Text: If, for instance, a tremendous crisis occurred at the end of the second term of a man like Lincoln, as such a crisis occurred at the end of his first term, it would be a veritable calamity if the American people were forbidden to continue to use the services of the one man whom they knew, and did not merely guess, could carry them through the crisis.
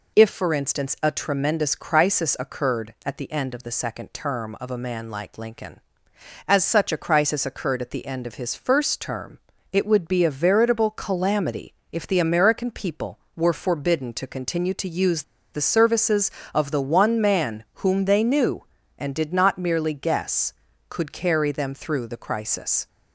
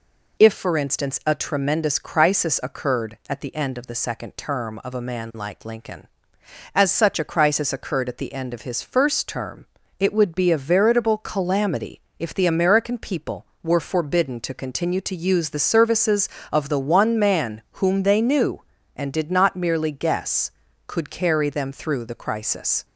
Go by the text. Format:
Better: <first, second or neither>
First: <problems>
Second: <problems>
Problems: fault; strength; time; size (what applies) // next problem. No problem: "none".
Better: second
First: pauses between "calamity" and "if"; slight; at 11.7 s; 0.18 s long // pauses between "use" and "the"; slight; at 15.2 s; 0.29 s long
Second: pauses between "calamity" and "if"; slight; at 12.0 s; 0.18 s long